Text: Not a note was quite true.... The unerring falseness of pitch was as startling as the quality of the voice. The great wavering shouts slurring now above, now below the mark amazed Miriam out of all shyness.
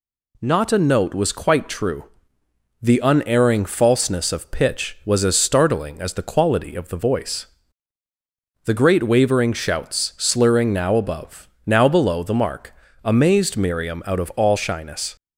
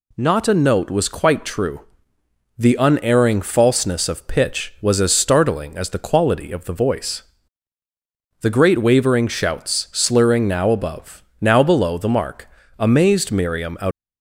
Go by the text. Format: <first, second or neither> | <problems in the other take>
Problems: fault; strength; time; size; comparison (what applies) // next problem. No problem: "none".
first | pauses between "mark" and "amazed"; slight; at 12.4 s; 0.30 s long; slight in the first // stops before "of all shyness"; at 13.9 s